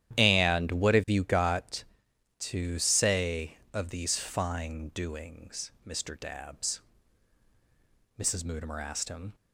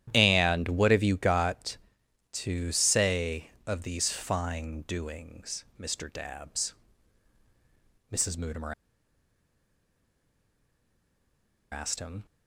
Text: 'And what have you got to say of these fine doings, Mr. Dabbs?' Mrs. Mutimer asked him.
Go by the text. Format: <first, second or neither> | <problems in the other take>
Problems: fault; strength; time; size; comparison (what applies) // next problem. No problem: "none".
first | starts louder than the rest; strong; until 1.1 s; 11 dB; strong in the first // pauses between "Mutimer" and "asked"; strong; at 8.7 s; 2.9 s long